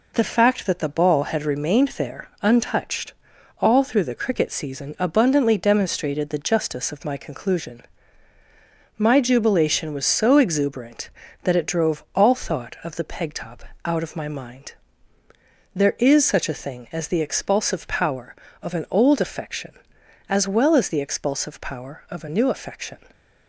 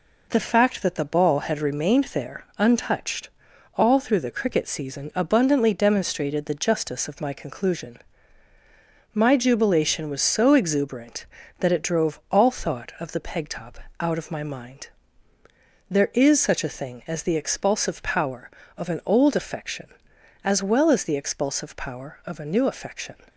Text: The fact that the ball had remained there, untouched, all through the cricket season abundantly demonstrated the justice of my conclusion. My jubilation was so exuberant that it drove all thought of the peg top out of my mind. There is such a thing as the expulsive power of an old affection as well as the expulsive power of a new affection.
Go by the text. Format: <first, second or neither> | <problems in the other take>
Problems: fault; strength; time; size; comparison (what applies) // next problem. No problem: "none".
neither | pauses between "top" and "out"; slight; the same in both